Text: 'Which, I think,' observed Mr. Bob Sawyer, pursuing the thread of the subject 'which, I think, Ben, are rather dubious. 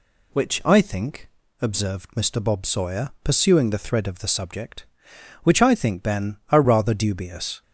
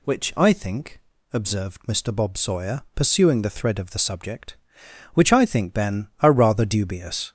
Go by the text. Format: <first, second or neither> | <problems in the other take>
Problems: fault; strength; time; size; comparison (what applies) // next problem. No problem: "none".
first | gets louder; noticeable; throughout; 4 dB